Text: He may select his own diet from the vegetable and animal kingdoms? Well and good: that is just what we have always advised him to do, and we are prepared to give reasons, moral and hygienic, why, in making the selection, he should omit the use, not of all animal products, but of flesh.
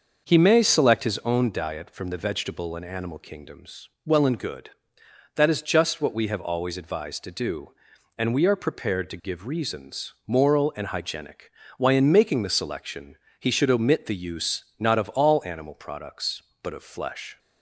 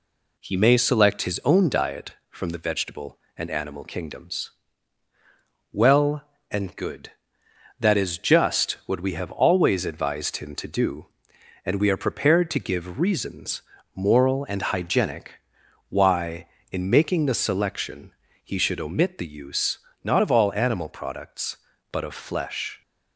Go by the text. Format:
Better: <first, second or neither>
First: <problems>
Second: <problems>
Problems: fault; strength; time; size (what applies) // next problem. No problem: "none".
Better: second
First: starts louder than the rest; until 1.2 s; 6 dB // skips "him"; at 7.2 s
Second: none